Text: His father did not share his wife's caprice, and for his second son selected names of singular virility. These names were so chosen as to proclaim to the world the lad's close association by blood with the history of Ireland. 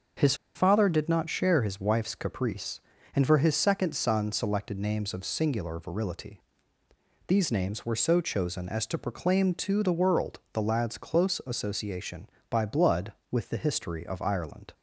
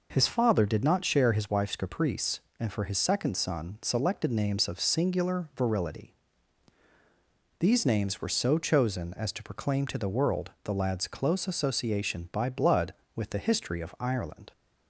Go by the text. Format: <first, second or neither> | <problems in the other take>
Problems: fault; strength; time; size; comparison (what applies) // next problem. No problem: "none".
second | starts louder than the rest; until 1.4 s; 6.5 dB // pauses between "His" and "father"; slight; at 0.3 s; 0.21 s long